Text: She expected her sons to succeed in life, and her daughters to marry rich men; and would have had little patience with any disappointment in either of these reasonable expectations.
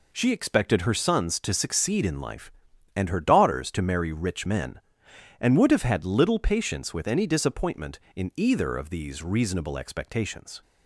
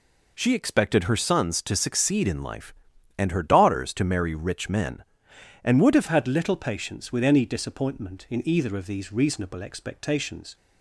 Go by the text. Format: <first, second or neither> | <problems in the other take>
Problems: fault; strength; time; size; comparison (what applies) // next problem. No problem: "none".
first | changes voice at "had"; from 6.0 s on; 4.5 s long